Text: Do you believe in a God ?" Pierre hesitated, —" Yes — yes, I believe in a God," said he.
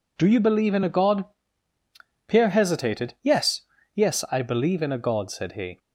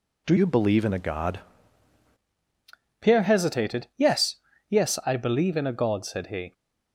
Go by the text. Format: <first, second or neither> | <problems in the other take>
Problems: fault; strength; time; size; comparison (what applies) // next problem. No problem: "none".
first | changes voice from "you" to "God"; from 0.3 to 1.3 s; 1.0 s long